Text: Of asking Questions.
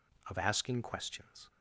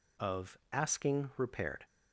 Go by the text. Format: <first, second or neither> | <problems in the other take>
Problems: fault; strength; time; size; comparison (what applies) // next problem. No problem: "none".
first | says "Repaired" for "Questions"; at 1.3 s